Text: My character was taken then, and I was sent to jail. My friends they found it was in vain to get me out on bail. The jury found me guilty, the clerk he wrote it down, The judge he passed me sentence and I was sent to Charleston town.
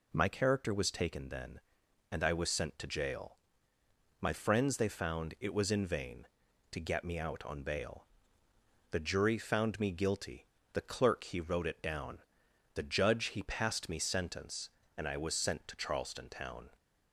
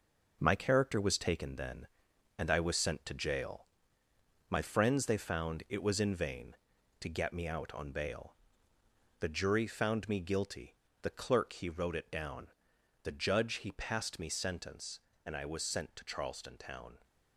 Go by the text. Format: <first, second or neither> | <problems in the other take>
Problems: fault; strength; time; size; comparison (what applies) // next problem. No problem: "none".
first | gets quieter; throughout; 6.5 dB